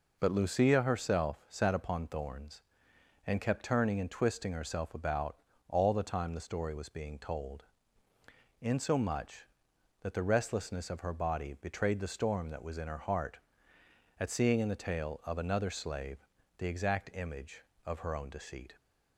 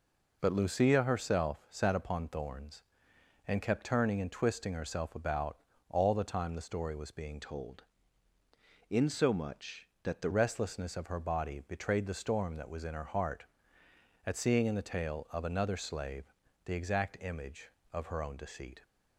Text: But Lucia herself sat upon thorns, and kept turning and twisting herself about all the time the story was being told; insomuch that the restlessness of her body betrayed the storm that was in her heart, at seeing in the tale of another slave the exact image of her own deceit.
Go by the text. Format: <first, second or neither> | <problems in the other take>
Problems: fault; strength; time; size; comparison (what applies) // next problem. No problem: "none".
first | pauses between "about" and "all"; slight; at 5.5 s; 0.32 s long; slight in the first // changes voice from "told" to "the"; from 7.4 to 10.2 s; 2.8 s long // pauses between "slave" and "the"; slight; at 16.3 s; 0.32 s long; slight in the first